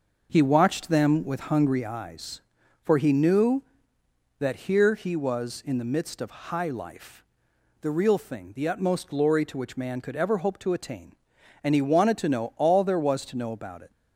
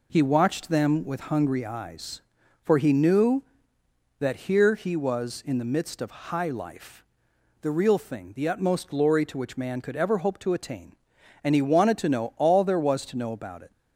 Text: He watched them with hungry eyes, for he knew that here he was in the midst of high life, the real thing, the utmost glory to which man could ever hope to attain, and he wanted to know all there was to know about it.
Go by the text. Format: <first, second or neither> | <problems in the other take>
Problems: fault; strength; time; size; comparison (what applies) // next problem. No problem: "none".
second | starts louder than the rest; until 2.0 s; 6 dB